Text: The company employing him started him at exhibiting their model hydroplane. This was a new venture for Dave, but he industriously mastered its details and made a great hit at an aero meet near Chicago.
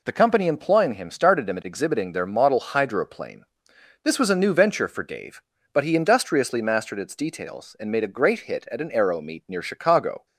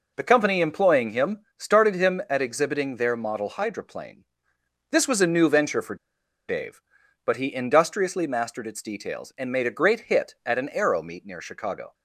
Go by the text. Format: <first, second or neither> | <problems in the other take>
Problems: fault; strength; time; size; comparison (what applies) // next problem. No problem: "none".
first | pauses between "him" and "started"; slight; at 1.3 s; 0.18 s long // pauses between "for" and "Dave"; noticeable; at 5.9 s; 0.52 s long